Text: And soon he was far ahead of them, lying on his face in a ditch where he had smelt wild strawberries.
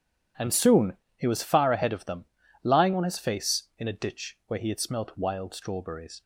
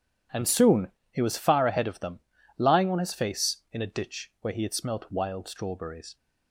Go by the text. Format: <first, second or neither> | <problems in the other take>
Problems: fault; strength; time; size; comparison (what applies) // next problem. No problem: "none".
neither | starts louder than the rest; strong; the same in both // pauses between "soon" and "he"; slight; the same in both